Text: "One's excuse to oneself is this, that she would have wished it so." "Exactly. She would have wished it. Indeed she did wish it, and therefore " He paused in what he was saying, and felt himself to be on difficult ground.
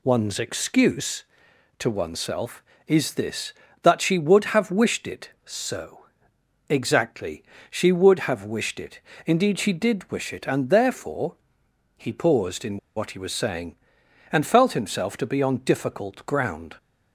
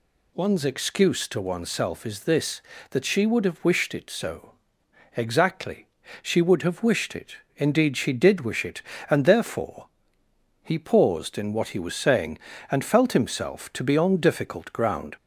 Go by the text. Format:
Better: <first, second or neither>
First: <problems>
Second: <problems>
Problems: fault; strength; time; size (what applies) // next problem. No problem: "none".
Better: second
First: pauses between "in" and "what"; slight; at 12.7 s; 0.19 s long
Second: none